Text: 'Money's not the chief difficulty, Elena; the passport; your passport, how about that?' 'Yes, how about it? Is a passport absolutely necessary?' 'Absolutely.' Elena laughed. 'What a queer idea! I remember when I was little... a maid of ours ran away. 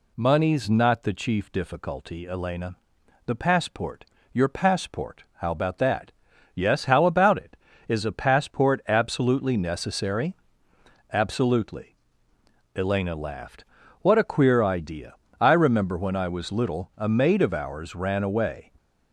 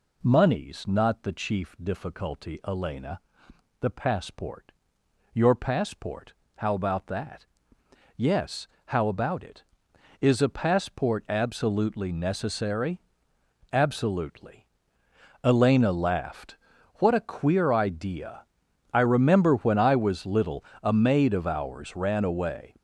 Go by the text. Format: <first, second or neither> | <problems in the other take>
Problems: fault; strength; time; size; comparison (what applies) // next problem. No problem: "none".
neither | none